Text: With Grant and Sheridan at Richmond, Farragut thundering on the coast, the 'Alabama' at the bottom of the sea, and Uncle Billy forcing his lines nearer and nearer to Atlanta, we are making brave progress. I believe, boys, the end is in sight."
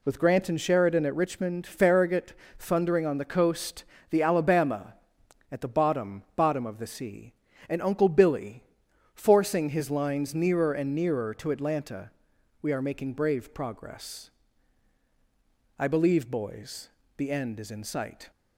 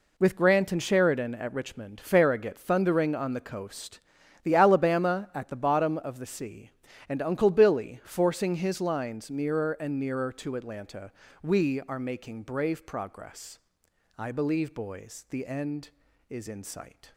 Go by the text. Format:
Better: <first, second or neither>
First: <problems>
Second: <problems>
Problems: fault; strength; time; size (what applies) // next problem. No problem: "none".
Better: second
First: pauses between "Farragut" and "thundering"; slight; at 2.3 s; 0.26 s long // says "bottom" twice; at 6.3 s // pauses between "Billy" and "forcing"; noticeable; at 8.6 s; 0.50 s long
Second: none